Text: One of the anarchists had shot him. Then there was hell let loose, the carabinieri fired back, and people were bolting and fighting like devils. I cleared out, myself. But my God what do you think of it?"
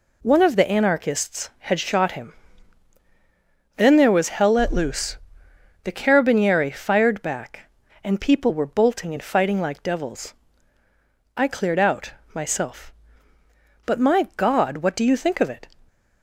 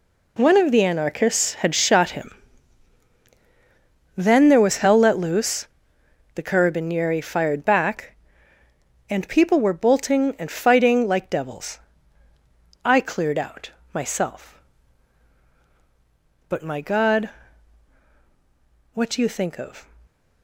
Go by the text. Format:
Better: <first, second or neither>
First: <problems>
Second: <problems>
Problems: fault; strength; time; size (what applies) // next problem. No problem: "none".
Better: first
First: none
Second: pauses between "God" and "what"; strong; at 17.3 s; 1.6 s long // stops before "it"; at 20.0 s